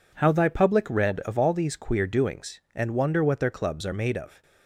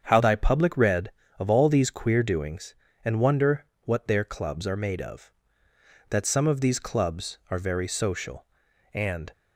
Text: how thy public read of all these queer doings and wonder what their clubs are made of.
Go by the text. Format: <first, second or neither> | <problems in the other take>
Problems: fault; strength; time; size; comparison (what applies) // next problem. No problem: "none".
first | starts louder than the rest; strong; until 1.0 s; 7.5 dB // pauses between "wonder" and "what"; slight; at 3.6 s; 0.20 s long // goes on to say "That some of these clubs are very social and"; strong; from 6.0 s on; 3.2 s long